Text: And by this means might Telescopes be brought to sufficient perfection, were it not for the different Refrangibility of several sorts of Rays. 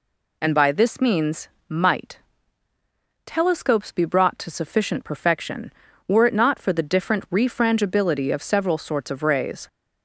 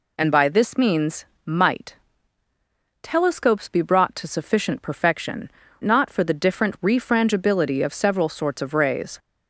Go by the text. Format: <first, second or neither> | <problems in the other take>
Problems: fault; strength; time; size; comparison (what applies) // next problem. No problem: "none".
first | pauses between "means" and "might"; slight; at 1.2 s; 0.20 s long; slight in the first // pauses between "might" and "Telescopes"; at 1.9 s; 1.0 s long; also in the first // skips "were it"; at 5.6 s